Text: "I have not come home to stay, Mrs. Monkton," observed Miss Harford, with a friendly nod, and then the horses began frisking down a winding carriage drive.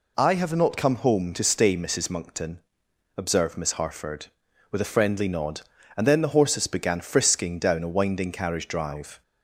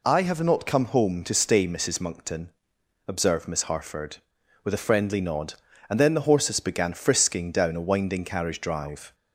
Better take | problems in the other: neither | none

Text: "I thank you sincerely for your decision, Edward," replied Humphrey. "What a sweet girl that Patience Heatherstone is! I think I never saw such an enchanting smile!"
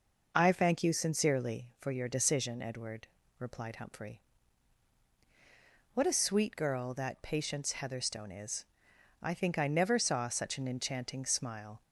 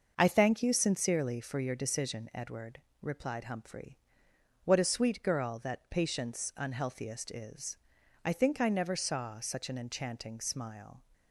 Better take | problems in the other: first | starts louder than the rest; until 1.1 s; 6 dB // says "Unhealthiest" for "Heatherstone"; at 6.5 s

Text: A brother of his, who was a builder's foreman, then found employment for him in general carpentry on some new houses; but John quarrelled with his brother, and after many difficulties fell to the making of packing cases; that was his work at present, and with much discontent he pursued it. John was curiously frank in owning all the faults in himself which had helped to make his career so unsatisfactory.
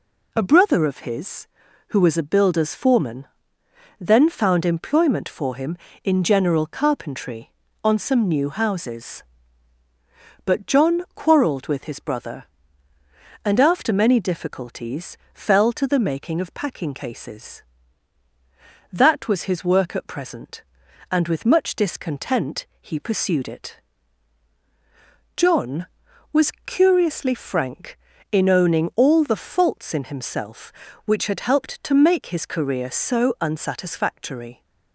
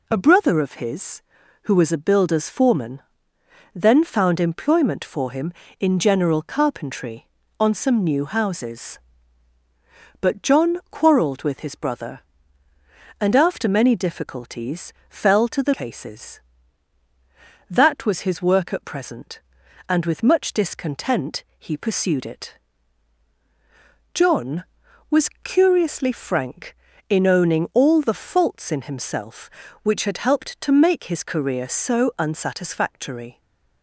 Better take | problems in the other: first | pauses between "difficulties" and "fell"; slight; at 14.9 s; 0.16 s long; slight in the first // skips "making of packing"; at 15.7 s // pauses between "discontent" and "he"; slight; at 21.4 s; 0.16 s long; slight in the first // stays silent after the last word; slight; from 33.3 s on; 0.5 s long

